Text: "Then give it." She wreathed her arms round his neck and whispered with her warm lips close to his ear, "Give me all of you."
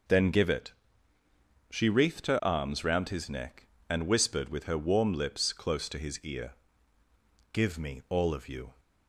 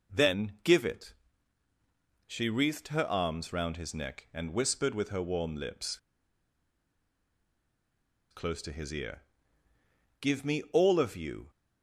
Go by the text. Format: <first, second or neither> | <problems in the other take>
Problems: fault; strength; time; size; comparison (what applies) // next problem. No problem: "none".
first | pauses between "lips" and "close"; strong; at 5.9 s; 2.3 s long